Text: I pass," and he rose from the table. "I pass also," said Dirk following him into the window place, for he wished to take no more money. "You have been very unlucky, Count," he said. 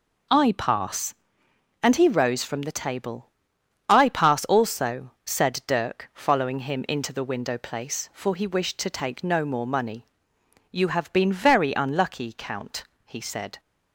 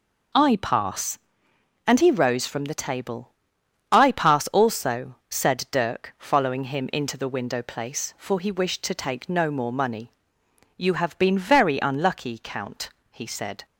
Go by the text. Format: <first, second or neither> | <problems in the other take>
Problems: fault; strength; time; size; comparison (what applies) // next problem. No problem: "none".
neither | none